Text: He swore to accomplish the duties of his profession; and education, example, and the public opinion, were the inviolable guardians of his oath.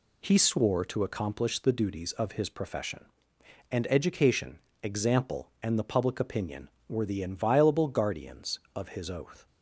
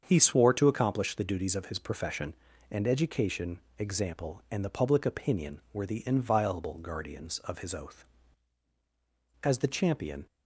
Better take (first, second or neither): first